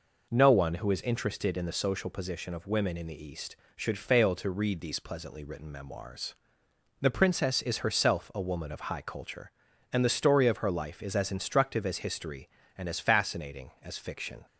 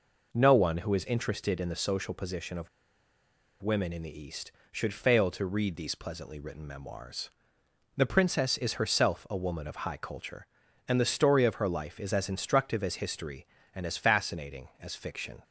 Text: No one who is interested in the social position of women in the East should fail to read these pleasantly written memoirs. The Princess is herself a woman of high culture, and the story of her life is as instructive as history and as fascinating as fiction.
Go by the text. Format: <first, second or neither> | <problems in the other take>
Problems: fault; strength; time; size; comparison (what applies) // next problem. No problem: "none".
first | pauses between "of" and "women"; noticeable; at 2.6 s; 0.94 s long